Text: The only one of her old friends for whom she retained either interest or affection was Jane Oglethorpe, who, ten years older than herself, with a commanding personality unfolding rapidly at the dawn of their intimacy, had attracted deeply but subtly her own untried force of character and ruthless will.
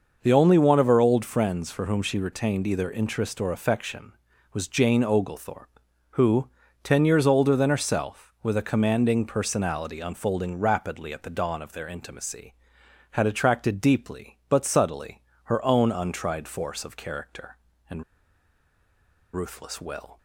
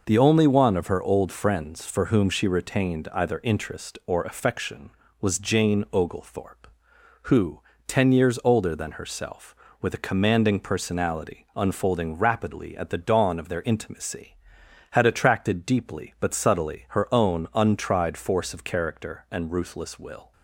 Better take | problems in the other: second | starts louder than the rest; noticeable; until 1.2 s; 6 dB // pauses between "subtly" and "her"; slight; at 15.2 s; 0.22 s long // pauses between "and" and "ruthless"; strong; at 18.0 s; 1.3 s long

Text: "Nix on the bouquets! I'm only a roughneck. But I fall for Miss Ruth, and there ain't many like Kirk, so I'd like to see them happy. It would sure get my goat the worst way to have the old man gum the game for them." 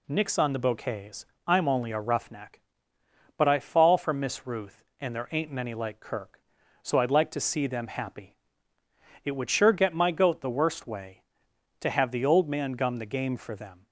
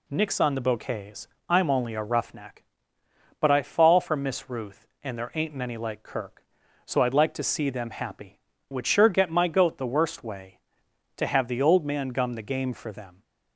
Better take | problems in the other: first | skips "It"; at 8.5 s

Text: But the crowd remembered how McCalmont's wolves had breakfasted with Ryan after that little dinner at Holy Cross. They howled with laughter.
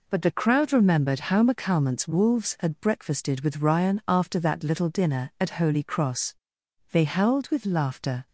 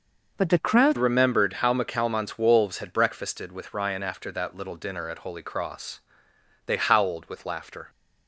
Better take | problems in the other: first | changes voice at "remembered"; from 0.9 s on; 6.9 s long

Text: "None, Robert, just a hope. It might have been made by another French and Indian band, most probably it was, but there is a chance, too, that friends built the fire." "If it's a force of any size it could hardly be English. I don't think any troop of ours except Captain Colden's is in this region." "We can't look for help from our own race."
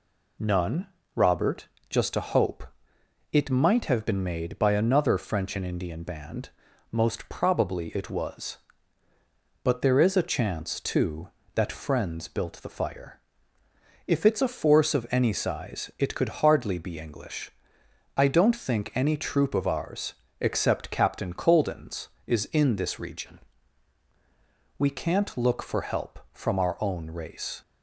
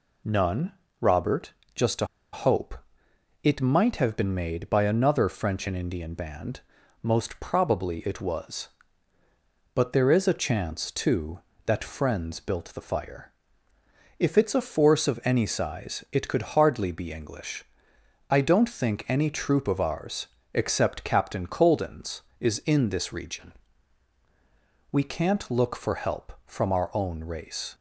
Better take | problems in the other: first | pauses between "a" and "hope"; slight; at 2.0 s; 0.27 s long // pauses between "ours" and "except"; slight; at 20.2 s; 0.26 s long; slight in the first

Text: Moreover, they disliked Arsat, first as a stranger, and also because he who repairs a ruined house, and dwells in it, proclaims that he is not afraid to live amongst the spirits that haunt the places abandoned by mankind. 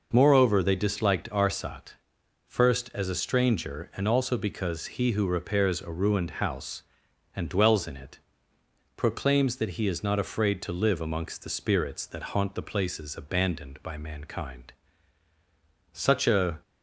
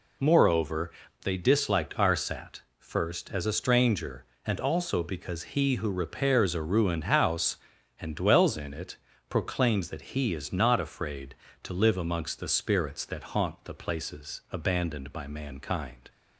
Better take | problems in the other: second | goes on to say "Such a"; noticeable; from 15.9 s on; 0.68 s long

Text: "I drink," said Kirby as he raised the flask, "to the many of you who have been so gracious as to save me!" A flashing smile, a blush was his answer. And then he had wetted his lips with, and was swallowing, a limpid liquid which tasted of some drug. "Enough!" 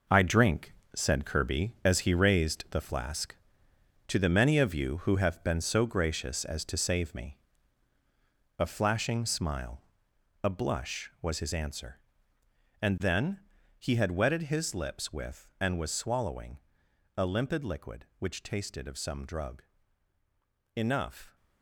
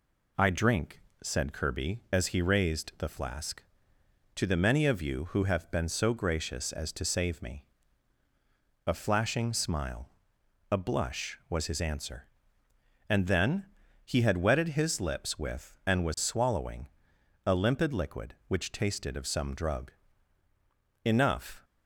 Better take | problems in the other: second | gets quieter; strong; throughout; 10 dB // pauses between "then" and "he"; slight; at 13.4 s; 0.36 s long; slight in the second

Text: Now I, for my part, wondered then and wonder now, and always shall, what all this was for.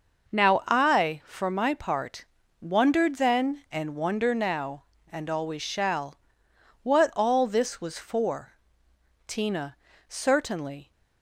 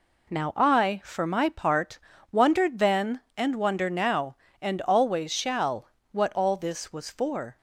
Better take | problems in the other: second | goes on to say "Tina certainly"; from 9.2 s on; 1.6 s long

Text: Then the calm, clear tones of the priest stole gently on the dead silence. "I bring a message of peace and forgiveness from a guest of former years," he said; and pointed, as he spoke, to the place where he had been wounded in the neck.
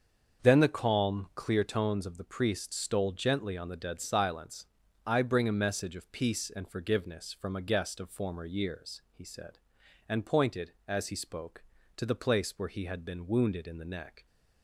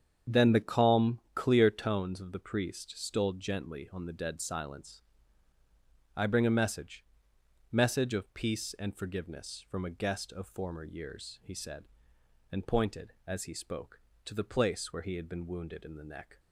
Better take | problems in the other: first | starts louder than the rest; strong; until 1.4 s; 8 dB; also in the first // says "message" twice; at 7.7 s

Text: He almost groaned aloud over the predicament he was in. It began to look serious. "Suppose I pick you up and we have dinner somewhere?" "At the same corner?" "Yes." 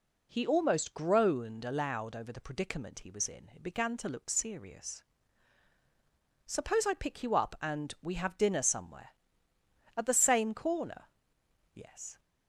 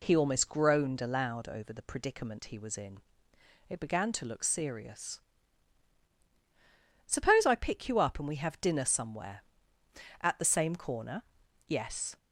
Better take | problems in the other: neither | none

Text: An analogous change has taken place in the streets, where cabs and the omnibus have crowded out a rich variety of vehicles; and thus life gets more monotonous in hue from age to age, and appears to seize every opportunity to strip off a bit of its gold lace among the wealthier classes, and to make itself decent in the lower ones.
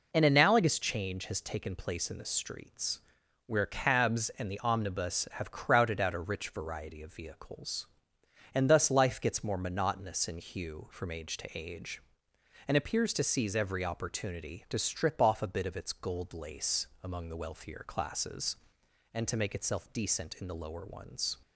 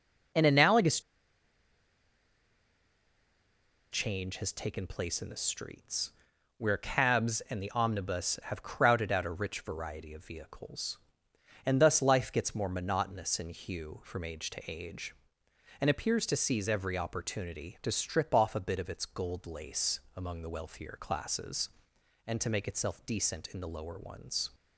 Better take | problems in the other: first | pauses between "analogous" and "change"; strong; at 1.0 s; 2.9 s long // pauses between "lace" and "among"; slight; at 19.9 s; 0.16 s long; slight in the first

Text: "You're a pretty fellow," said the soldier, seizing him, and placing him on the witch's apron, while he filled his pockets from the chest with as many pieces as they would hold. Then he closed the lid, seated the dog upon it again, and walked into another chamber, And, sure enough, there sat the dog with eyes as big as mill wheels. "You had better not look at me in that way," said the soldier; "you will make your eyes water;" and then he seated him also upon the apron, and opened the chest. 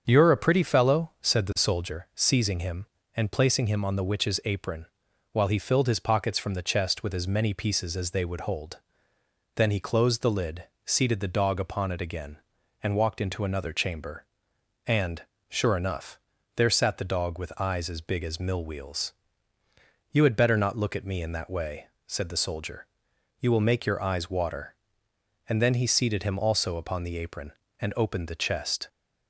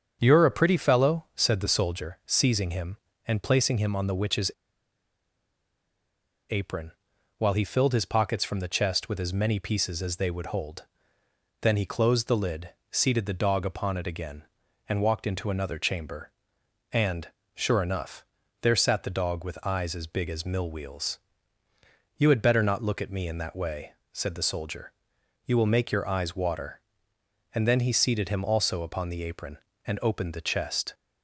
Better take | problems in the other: first | starts louder than the rest; strong; until 1.2 s; 7.5 dB; strong in the first // pauses between "witch's" and "apron"; strong; at 4.5 s; 2.0 s long

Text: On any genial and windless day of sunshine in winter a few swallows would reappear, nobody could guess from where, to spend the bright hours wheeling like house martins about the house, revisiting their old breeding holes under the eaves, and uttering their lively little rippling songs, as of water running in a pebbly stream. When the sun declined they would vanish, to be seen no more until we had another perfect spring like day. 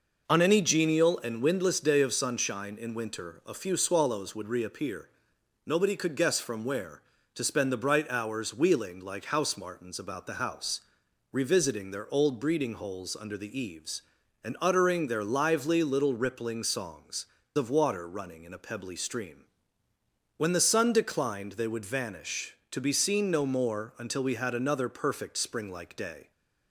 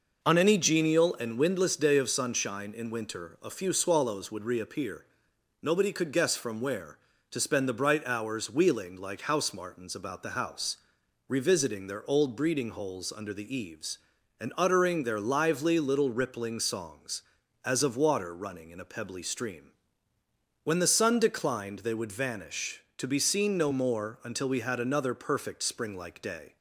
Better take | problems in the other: second | skips "as"; at 17.4 s

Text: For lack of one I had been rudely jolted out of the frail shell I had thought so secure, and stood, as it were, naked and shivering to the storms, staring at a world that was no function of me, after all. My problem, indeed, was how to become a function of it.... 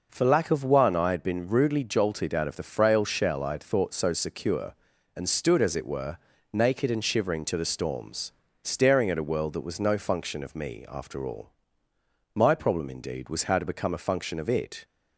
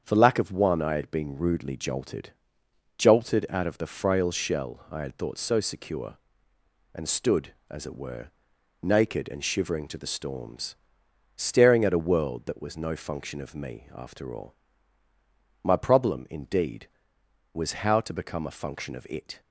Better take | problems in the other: first | starts louder than the rest; strong; until 1.0 s; 7.5 dB // says "jolted" twice; at 2.9 s

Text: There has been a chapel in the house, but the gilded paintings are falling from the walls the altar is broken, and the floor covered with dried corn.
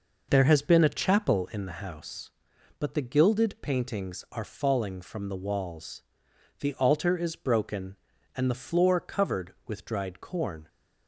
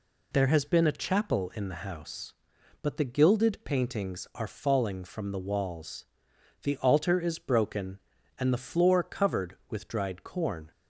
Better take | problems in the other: second | starts louder than the rest; noticeable; until 1.6 s; 5.5 dB // pauses between "walls" and "the"; noticeable; at 6.0 s; 0.58 s long; noticeable in the second

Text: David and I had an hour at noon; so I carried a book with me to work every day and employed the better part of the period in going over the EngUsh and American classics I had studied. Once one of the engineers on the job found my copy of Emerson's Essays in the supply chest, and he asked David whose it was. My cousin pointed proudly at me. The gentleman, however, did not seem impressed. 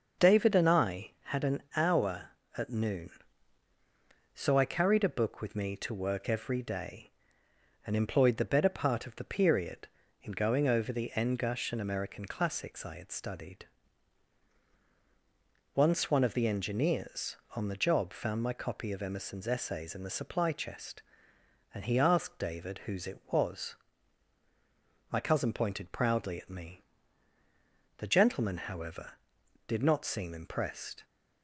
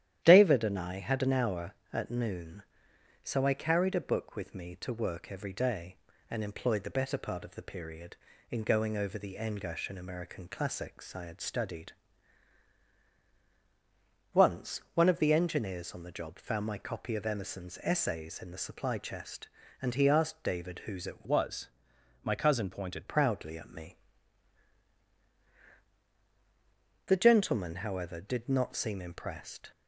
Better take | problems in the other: first | starts louder than the rest; strong; until 1.2 s; 11 dB; also in the first // changes voice from "was" to "pointed"; from 21.2 to 23.0 s; 1.8 s long

